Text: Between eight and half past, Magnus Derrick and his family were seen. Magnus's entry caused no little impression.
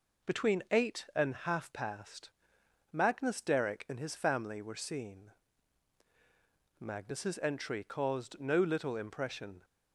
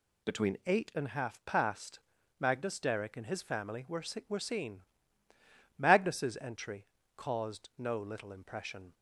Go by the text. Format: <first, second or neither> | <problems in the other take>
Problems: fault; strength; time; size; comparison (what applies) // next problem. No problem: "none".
first | says "were" twice; at 4.2 s // pauses between "entry" and "caused"; slight; at 6.8 s; 0.32 s long